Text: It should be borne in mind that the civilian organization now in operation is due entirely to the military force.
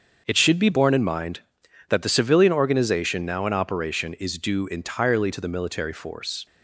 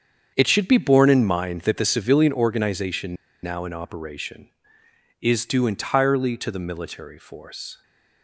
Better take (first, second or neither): first